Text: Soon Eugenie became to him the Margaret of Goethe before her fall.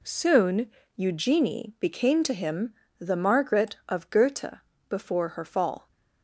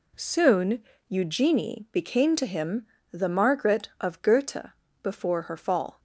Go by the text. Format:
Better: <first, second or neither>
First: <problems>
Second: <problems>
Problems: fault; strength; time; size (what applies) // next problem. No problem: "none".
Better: neither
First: pauses between "Soon" and "Eugenie"; slight; at 0.6 s; 0.28 s long // pauses between "him" and "the"; slight; at 2.7 s; 0.24 s long // pauses between "Goethe" and "before"; slight; at 4.5 s; 0.32 s long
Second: pauses between "Soon" and "Eugenie"; slight; at 0.8 s; 0.28 s long // pauses between "him" and "the"; slight; at 2.8 s; 0.24 s long // pauses between "Goethe" and "before"; slight; at 4.6 s; 0.34 s long